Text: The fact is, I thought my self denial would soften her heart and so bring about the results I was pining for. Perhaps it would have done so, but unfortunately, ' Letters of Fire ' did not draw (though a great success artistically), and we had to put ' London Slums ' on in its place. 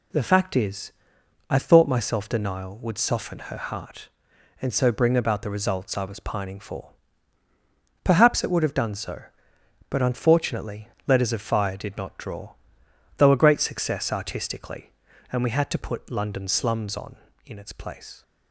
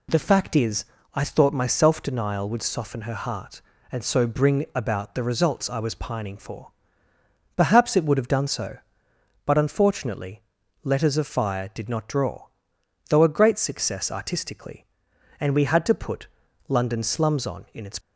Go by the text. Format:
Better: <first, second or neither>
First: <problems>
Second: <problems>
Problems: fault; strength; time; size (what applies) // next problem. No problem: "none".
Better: first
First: none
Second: stops before "place"; at 18.0 s